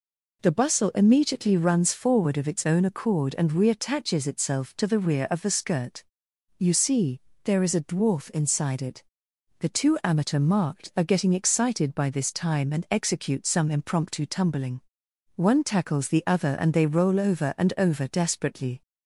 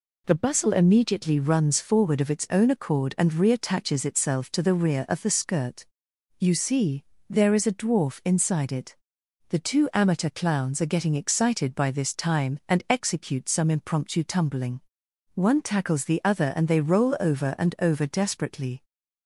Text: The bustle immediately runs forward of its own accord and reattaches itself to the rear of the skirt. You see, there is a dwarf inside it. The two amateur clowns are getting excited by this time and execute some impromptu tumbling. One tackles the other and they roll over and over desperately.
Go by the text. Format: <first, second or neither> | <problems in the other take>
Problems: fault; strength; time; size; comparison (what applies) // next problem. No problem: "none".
second | says "marked" for "clowns"; at 10.3 s